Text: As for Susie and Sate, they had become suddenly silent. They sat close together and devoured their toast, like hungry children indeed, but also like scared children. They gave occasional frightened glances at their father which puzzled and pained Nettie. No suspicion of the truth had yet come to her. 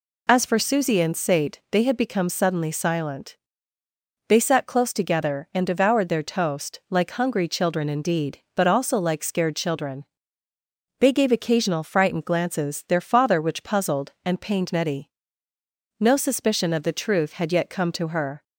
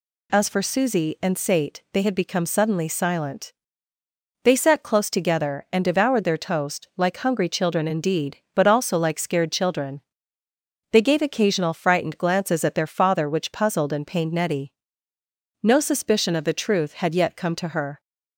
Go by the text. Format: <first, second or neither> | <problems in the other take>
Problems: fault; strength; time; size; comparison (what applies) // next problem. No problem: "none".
second | skips "at"; at 12.8 s